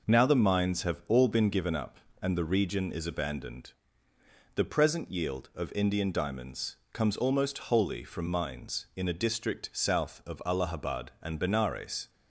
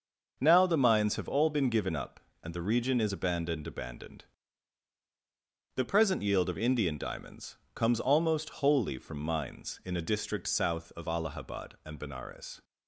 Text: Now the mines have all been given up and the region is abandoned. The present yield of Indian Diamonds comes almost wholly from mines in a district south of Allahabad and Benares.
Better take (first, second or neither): first